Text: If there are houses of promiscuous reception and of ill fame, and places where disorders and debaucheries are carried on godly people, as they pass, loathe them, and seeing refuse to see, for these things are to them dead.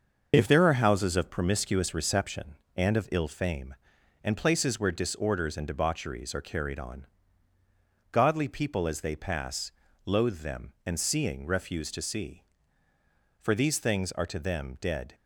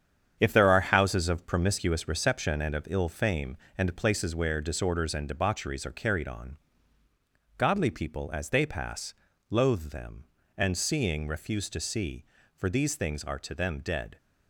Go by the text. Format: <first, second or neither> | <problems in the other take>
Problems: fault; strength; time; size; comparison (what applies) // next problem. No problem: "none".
first | gets quieter; strong; throughout; 7.5 dB // pauses between "on" and "godly"; at 6.5 s; 1.0 s long; also in the first